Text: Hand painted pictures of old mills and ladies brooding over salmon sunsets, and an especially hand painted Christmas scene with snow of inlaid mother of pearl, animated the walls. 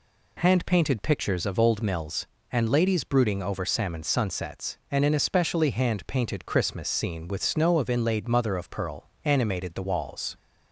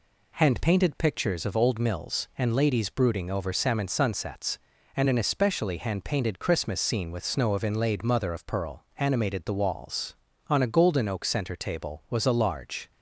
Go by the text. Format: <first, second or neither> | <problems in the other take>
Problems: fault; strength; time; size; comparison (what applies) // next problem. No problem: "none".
first | goes on to say "On a golden oak center table was a large"; strong; from 10.5 s on; 2.4 s long